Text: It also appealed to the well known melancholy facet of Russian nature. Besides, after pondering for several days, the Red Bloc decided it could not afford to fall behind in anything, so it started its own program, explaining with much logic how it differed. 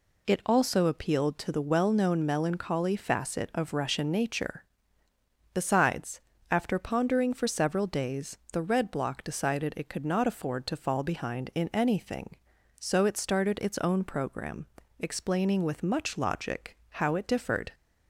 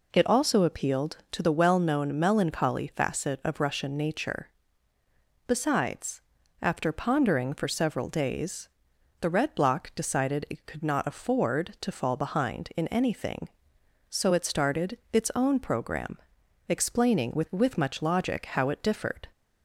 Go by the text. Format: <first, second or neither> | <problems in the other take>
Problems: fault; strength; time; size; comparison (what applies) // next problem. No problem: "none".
first | says "with" twice; at 17.5 s